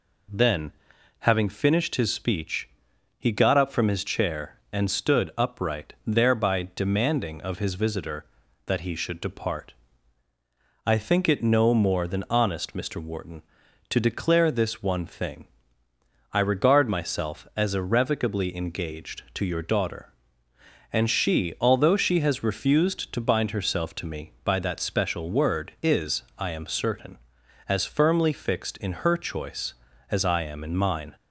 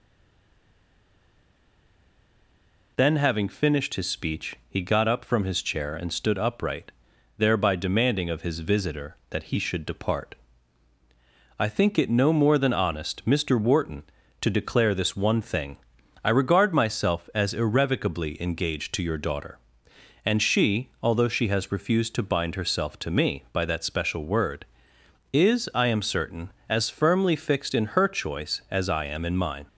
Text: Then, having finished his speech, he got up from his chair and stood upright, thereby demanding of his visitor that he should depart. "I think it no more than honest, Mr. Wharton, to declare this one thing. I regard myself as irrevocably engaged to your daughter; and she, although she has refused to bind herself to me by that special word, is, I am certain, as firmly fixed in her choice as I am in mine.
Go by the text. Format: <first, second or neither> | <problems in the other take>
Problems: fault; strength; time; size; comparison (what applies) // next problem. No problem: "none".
first | stays silent before the first word; strong; until 2.9 s; 2.9 s long